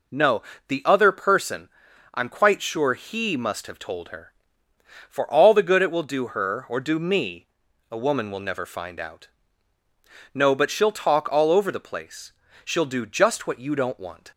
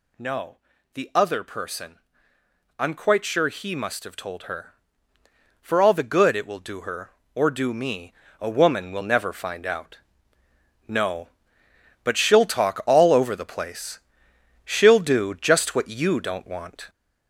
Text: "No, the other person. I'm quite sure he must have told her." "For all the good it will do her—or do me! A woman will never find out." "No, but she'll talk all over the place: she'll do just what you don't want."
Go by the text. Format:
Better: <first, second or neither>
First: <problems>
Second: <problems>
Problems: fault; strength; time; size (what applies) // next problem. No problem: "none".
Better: first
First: none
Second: gets louder; noticeable; throughout; 5.5 dB